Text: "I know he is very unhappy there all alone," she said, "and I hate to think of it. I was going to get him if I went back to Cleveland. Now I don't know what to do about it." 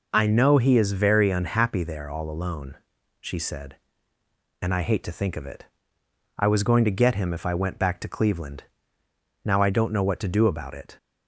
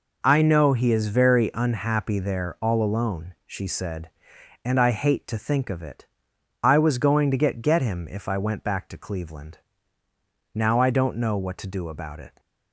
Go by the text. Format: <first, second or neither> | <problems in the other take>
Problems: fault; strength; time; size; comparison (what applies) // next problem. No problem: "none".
first | says "get" twice; at 7.6 s